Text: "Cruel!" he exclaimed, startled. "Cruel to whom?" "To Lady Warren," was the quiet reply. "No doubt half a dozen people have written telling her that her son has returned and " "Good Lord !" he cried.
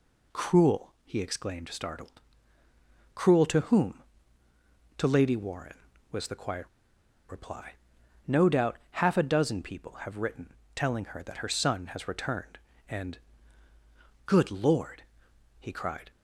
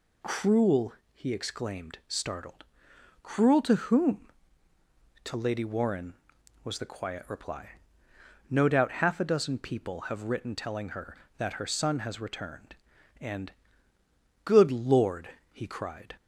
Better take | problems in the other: second | pauses between "quiet" and "reply"; noticeable; at 6.6 s; 0.62 s long // pauses between "written" and "telling"; slight; at 10.5 s; 0.22 s long

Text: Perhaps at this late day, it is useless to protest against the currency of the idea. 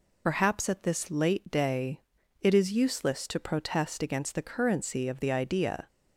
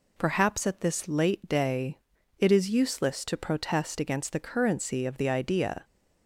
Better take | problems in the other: second | loses the start of "Perhaps"; at 0.2 s; 45 ms

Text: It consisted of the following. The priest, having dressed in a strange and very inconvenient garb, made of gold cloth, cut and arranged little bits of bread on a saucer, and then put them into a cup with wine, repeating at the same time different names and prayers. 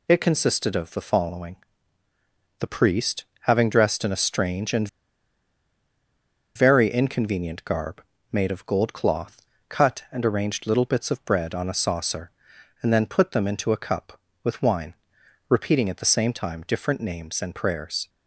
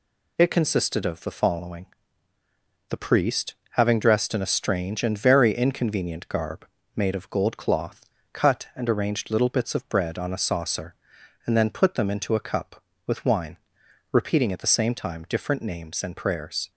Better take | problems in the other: second | pauses between "and" and "very"; strong; at 4.8 s; 1.6 s long

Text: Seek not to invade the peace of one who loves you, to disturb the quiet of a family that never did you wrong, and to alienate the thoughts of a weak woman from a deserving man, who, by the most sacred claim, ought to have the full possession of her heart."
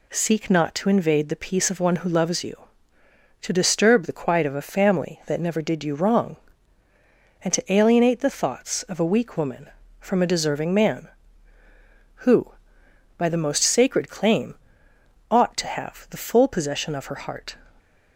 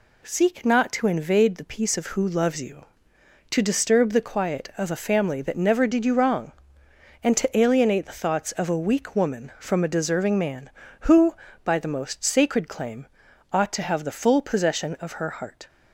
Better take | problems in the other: first | skips "one"; at 2.1 s

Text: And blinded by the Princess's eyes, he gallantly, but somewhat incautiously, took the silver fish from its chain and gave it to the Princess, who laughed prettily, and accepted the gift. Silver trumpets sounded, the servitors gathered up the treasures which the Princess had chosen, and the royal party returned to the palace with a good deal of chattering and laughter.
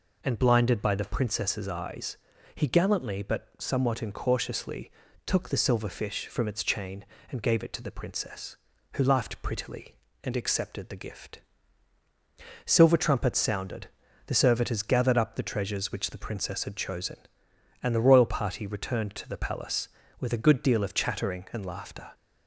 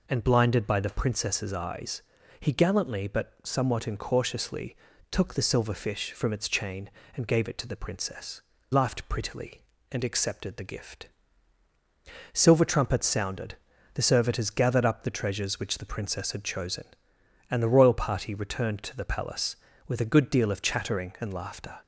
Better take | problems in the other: first | skips "who"; at 8.5 s

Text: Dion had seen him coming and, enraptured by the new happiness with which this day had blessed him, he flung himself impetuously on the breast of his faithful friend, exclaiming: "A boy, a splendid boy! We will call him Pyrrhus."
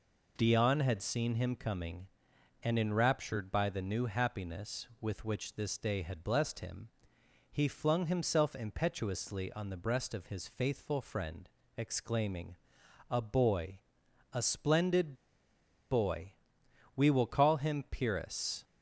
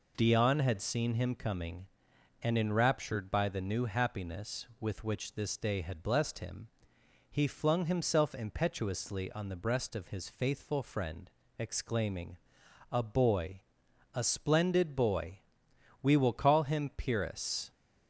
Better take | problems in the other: second | pauses between "splendid" and "boy"; noticeable; at 15.1 s; 0.76 s long

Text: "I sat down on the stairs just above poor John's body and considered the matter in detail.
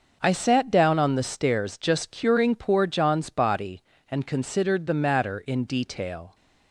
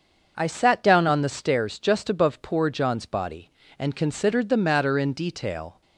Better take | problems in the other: second | starts louder than the rest; until 1.2 s; 6.5 dB; also in the second // says "curing" for "above"; at 2.1 s

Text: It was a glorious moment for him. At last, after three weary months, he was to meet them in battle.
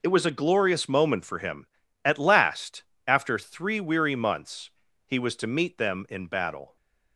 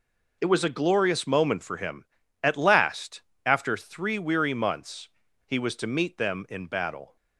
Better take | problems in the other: neither | none

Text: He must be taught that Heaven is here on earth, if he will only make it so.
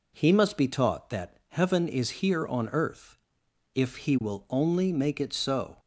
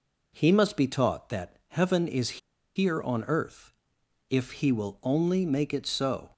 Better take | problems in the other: first | pauses between "is" and "here"; at 2.3 s; 0.37 s long

